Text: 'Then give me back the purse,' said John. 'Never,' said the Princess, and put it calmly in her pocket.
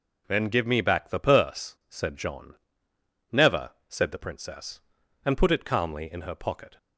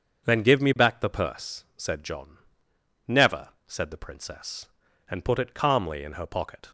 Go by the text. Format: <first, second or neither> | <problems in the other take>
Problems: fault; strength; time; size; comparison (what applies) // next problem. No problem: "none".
neither | none